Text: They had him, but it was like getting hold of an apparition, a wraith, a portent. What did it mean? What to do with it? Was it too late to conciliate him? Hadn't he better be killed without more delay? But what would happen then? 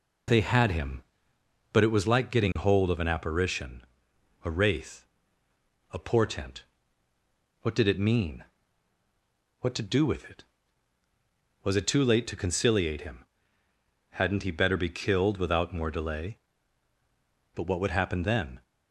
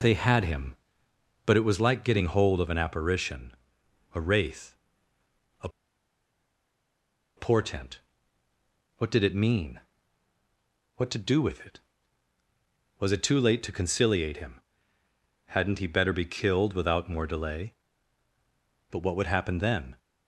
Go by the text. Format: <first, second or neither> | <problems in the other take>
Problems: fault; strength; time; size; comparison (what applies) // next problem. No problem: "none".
first | pauses between "a" and "portent"; strong; at 5.6 s; 1.6 s long